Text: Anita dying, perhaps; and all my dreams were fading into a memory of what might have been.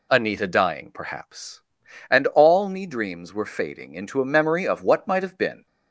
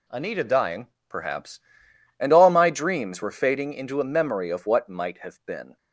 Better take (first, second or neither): second